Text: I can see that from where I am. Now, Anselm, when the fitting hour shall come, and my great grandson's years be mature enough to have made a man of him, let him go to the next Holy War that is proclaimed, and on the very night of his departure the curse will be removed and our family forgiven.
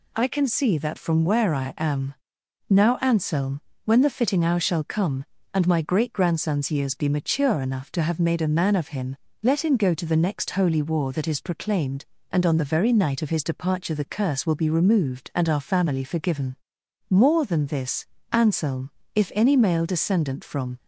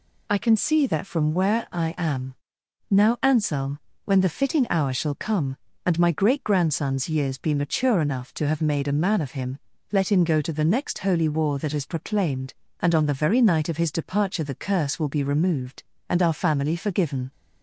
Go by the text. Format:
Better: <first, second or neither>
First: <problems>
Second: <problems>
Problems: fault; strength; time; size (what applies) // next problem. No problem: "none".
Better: second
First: goes on to say "More than this Anselm if any male descendant from"; strong; from 17.0 s on; 3.6 s long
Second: none